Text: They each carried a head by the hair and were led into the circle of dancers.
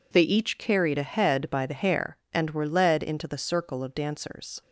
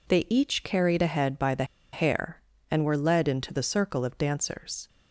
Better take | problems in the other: first | pauses between "the" and "hair"; slight; at 1.6 s; 0.29 s long

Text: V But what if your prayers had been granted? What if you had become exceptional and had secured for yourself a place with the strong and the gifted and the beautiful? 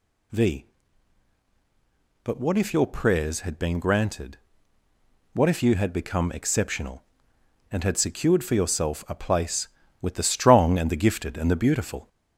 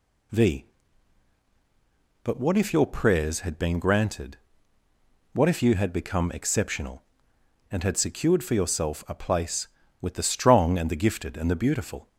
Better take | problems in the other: second | gets louder; slight; throughout; 3 dB

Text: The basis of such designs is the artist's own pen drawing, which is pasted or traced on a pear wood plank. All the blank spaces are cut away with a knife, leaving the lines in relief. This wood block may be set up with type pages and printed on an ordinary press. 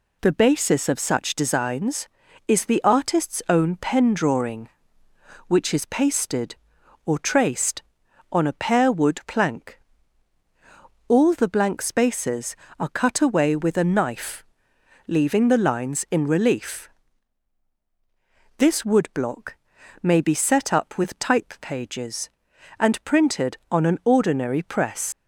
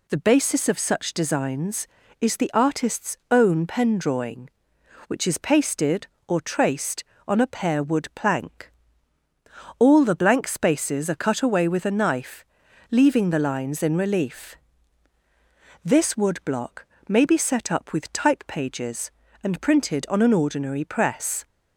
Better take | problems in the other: second | pauses between "block" and "may"; noticeable; at 19.5 s; 0.48 s long; slight in the second // leaves "press" unfinished; at 25.1 s; 85 ms

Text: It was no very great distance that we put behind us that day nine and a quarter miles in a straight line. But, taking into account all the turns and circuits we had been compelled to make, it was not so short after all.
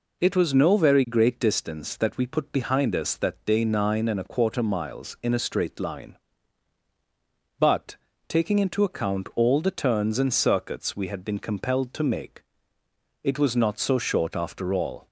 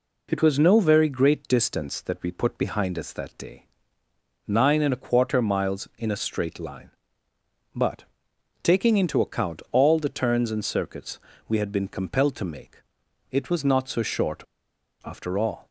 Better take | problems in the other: first | pauses between "day" and "nine"; noticeable; at 3.6 s; 0.80 s long // pauses between "circuits" and "we"; slight; at 11.1 s; 0.28 s long // pauses between "short" and "after"; noticeable; at 14.4 s; 0.63 s long

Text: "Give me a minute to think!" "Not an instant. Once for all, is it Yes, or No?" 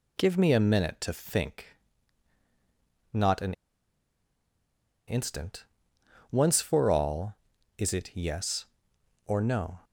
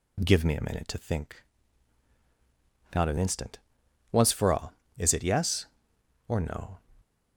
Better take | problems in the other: second | pauses between "an" and "instant"; strong; at 3.5 s; 1.5 s long

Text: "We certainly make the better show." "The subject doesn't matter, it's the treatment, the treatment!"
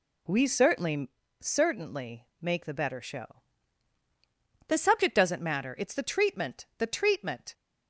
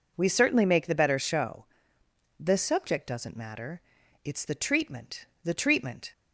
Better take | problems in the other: second | says "certainly" twice; at 1.4 s

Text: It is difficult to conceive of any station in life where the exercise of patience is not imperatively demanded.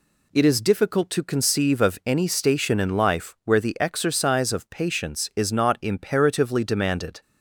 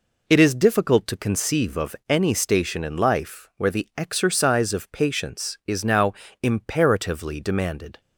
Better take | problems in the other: first | pauses between "of" and "any"; slight; at 1.9 s; 0.16 s long // says "now" for "not"; at 5.8 s

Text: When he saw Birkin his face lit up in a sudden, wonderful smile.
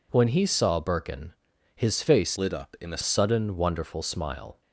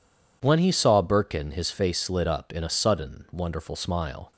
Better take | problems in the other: second | pauses between "Birkin" and "his"; at 1.3 s; 0.42 s long // changes voice from "lit" to "a"; from 2.3 to 3.0 s; 0.7 s long

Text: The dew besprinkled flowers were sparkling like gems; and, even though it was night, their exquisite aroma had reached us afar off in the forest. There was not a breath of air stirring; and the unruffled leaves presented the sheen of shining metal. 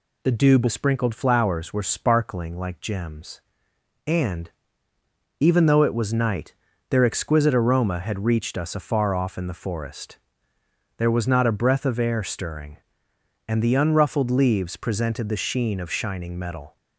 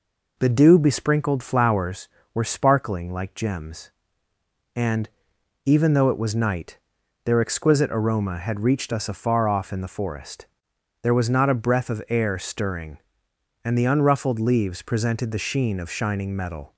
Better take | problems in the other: neither | none

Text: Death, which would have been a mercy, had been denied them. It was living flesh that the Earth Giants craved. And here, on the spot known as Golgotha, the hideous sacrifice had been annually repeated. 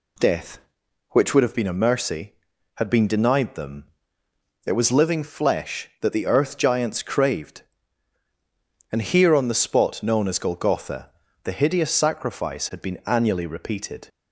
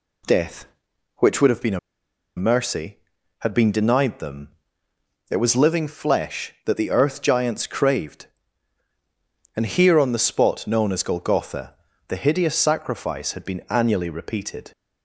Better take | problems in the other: first | pauses between "a" and "mercy"; noticeable; at 1.7 s; 0.58 s long

